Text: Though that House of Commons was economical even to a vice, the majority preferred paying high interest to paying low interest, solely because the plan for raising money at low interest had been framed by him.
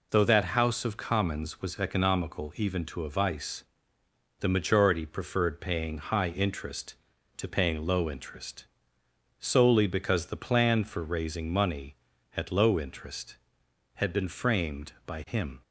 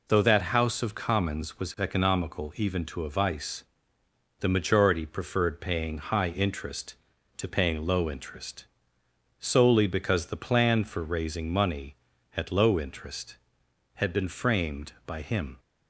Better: neither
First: none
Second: none

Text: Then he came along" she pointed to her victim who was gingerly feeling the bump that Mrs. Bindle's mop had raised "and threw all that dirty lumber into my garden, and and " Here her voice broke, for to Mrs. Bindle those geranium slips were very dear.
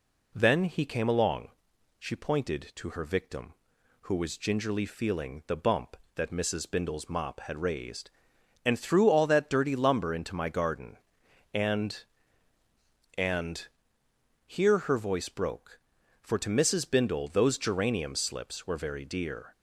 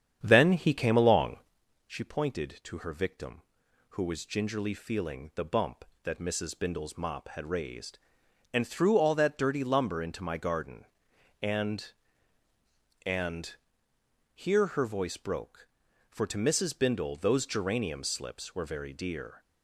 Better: first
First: pauses between "along" and "she"; noticeable; at 1.4 s; 0.50 s long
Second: starts louder than the rest; strong; until 1.6 s; 8.5 dB // pauses between "along" and "she"; noticeable; at 1.3 s; 0.50 s long

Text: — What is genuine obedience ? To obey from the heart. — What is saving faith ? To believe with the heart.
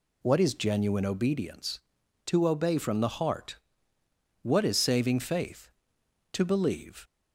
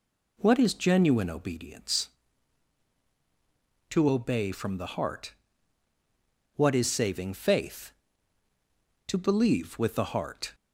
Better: second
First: stops before "with the heart"; at 7.0 s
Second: none

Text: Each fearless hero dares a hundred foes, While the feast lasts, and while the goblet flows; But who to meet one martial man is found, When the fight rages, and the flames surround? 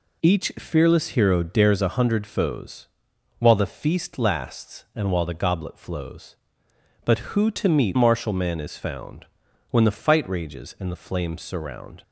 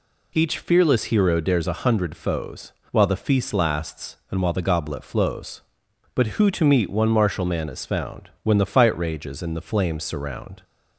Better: second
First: skips "one"; at 7.9 s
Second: none

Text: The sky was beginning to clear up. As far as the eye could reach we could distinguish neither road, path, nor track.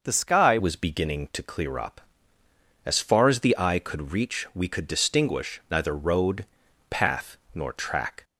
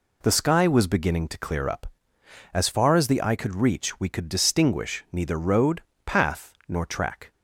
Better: second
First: changes voice at "was"; from 0.5 s on; 7.7 s long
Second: none

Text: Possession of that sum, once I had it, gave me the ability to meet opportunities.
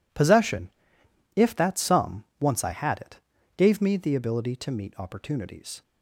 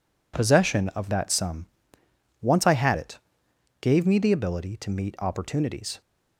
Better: second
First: says "if" for "of"; at 1.3 s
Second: none

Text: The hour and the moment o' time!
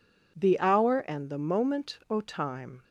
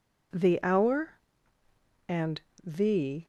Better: first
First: none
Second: pauses between "and" and "the"; slight; at 2.4 s; 0.22 s long // stops before "moment o time"; at 3.2 s

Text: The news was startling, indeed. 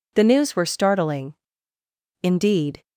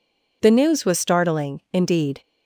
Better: second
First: says "were" for "was"; at 0.5 s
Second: none

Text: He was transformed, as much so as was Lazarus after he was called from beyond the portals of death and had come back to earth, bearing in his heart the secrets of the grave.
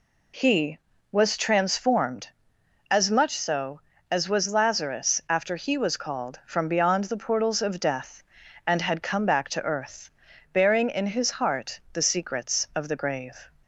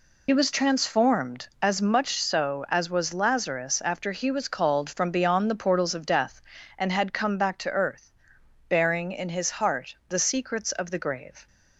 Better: first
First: none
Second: loses the start of "He"; at 0.2 s; 55 ms

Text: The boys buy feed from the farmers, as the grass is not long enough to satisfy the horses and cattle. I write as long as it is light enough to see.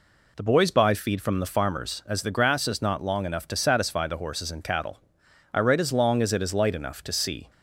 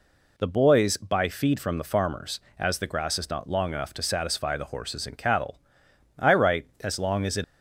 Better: first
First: none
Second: stops before "is light enough to see"; at 7.4 s

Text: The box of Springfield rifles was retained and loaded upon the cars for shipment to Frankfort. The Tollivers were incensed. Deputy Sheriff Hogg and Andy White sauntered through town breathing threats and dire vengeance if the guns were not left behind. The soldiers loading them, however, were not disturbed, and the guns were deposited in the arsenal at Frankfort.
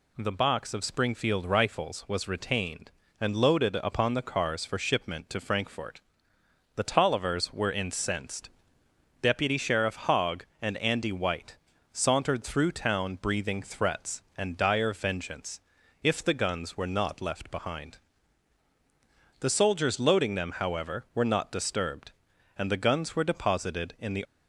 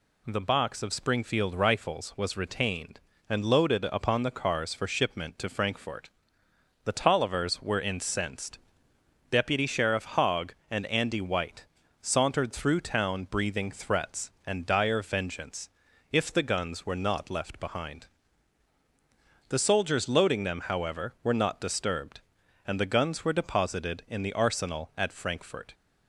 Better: second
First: pauses between "White" and "sauntered"; slight; at 11.5 s; 0.34 s long // pauses between "vengeance" and "if"; at 15.5 s; 0.42 s long // stops before "arsenal at Frankfort"; at 24.2 s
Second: pauses between "White" and "sauntered"; slight; at 11.6 s; 0.34 s long // pauses between "vengeance" and "if"; at 15.6 s; 0.42 s long

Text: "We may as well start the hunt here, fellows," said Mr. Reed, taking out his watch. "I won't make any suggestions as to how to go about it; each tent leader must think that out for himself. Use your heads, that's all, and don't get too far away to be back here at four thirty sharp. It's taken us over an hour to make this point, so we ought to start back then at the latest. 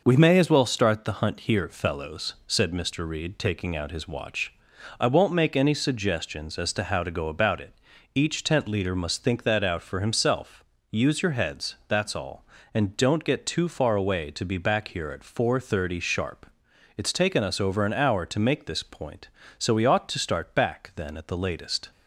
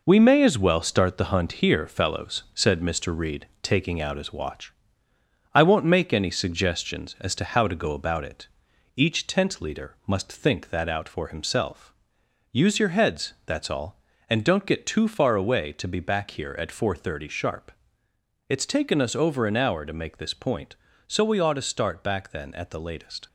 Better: first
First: none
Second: gets quieter; throughout; 6.5 dB

